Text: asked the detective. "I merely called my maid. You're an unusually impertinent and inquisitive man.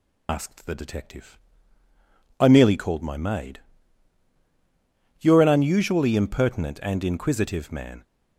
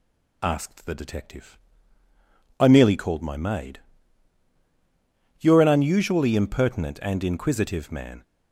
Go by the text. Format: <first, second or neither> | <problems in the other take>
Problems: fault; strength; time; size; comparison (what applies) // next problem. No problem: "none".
second | loses the start of "asked"; at 0.2 s; 75 ms